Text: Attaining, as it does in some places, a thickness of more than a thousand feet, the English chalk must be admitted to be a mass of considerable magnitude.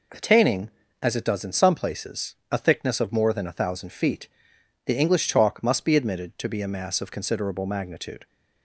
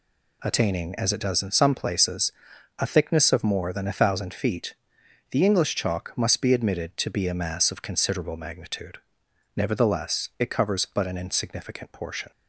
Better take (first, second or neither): first